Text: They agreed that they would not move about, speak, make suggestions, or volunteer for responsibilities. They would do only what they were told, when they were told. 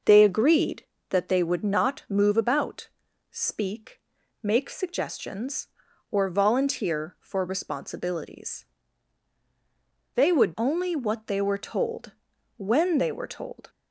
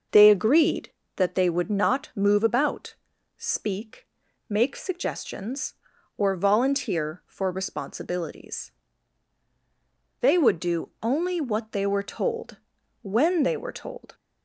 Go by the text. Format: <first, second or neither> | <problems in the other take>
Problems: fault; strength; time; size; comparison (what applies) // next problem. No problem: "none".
second | skips "do"; at 10.5 s